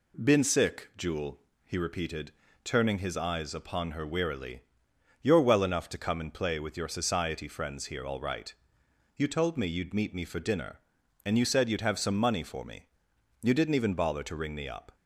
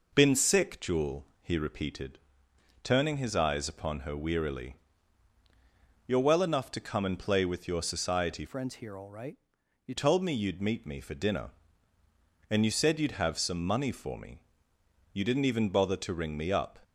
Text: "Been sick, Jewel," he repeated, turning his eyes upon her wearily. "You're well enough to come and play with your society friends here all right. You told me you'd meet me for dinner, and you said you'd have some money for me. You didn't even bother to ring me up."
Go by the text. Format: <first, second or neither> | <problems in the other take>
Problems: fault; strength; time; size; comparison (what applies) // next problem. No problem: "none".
first | changes voice from "friends" to "You"; from 8.4 to 9.9 s; 1.5 s long